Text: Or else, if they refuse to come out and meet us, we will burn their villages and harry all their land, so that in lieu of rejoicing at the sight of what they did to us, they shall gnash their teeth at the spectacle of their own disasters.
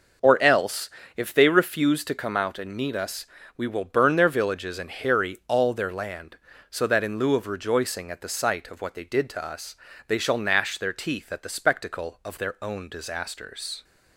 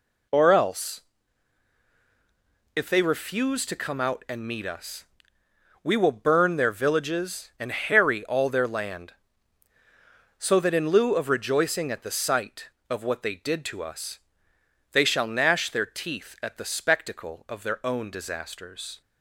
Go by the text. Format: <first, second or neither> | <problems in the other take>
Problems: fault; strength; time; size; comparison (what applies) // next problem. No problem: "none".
neither | none